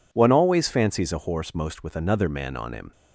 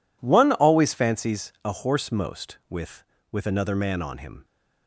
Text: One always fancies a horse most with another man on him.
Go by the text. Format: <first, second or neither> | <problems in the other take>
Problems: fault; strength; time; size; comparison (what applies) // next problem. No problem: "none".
first | says "with" twice; at 3.3 s